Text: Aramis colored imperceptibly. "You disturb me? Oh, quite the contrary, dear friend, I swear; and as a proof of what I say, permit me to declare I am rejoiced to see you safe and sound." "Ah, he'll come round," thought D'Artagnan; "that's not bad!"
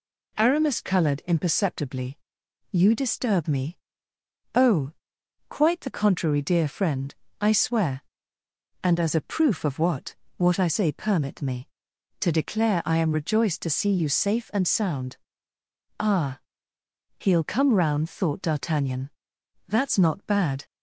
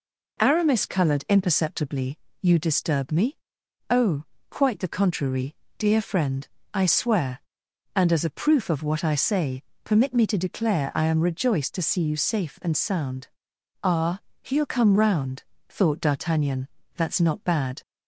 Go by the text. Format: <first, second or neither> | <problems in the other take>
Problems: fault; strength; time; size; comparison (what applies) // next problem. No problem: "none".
second | says "what" twice; at 10.3 s